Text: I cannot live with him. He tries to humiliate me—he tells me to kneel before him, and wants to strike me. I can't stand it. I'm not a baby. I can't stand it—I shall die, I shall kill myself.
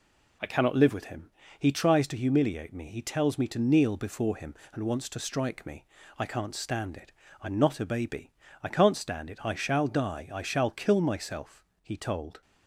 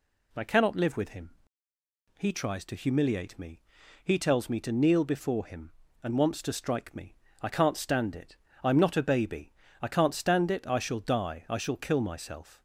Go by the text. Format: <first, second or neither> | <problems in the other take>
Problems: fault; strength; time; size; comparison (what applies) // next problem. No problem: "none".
second | goes on to say "He told"; from 11.8 s on; 0.58 s long